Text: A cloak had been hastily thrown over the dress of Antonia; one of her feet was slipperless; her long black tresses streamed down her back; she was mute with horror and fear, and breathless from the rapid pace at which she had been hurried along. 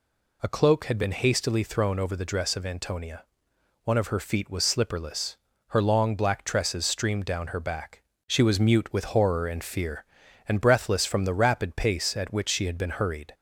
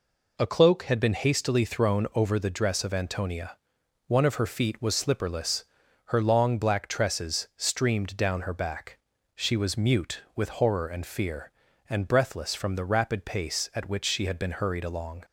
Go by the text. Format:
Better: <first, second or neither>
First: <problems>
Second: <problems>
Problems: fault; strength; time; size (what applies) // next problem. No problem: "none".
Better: second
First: stops before "along"; at 13.3 s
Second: none